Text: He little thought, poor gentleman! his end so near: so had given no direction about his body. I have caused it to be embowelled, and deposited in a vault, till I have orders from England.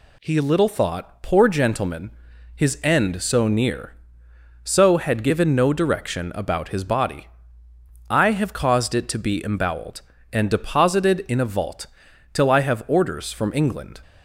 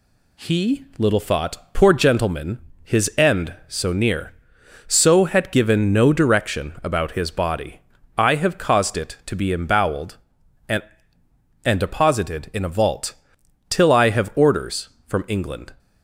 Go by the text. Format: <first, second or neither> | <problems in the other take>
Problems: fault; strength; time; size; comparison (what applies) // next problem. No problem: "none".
first | says "and" twice; at 11.6 s